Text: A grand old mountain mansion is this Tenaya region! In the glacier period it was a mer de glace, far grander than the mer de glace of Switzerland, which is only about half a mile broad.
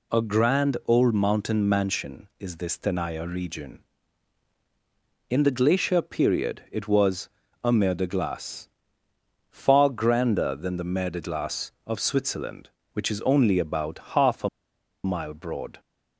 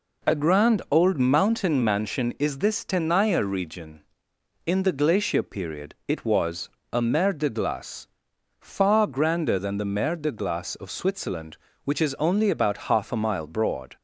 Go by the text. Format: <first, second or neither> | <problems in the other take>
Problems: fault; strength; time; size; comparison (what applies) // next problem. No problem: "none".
second | pauses between "was" and "a"; slight; at 7.2 s; 0.32 s long; slight in the second // pauses between "about" and "half"; slight; at 13.9 s; 0.16 s long // pauses between "a" and "mile"; noticeable; at 14.4 s; 0.55 s long